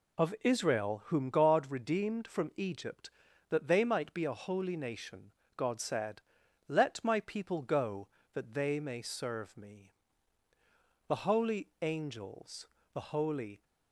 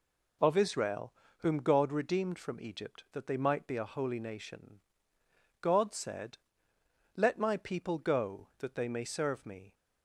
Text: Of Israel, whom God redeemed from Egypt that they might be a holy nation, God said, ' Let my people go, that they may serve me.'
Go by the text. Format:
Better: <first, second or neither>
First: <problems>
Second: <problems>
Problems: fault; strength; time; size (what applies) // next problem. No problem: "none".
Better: second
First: goes on to say "The holy angels the holy"; strong; from 11.0 s on; 2.5 s long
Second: none